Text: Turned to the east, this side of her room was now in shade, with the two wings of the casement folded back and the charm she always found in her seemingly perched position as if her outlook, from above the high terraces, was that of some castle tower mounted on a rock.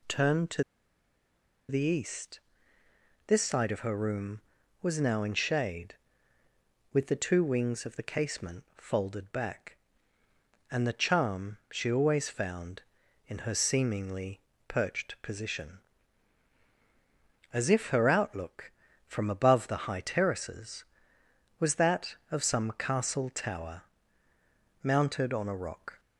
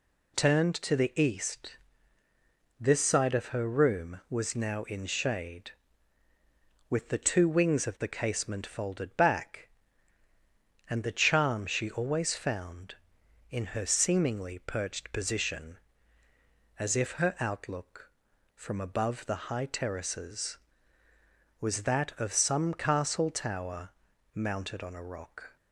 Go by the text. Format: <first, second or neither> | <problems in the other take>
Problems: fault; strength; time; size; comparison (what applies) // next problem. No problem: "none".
second | pauses between "to" and "the"; at 0.6 s; 1.0 s long // pauses between "seemingly" and "perched"; slight; at 14.3 s; 0.28 s long // pauses between "tower" and "mounted"; at 23.8 s; 1.0 s long; noticeable in the second